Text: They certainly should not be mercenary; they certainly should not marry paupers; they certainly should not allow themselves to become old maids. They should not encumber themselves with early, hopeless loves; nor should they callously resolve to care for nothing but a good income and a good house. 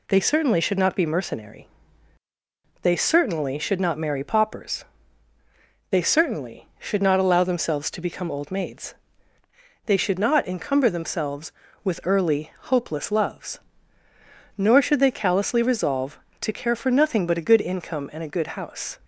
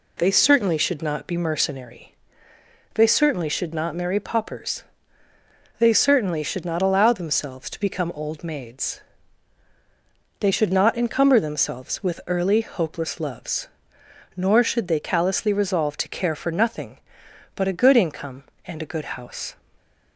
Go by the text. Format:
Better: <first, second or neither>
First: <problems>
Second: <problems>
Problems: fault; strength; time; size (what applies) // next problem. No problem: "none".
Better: neither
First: none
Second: none